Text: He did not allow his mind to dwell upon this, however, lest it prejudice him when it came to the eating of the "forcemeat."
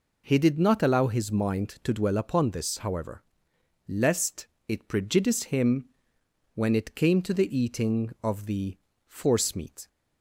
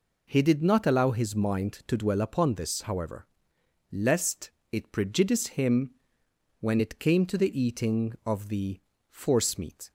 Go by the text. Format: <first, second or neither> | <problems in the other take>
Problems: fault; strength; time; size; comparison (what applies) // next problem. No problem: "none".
neither | pauses between "lest" and "it"; slight; the same in both // pauses between "him" and "when"; noticeable; the same in both // pauses between "the" and "forcemeat"; slight; the same in both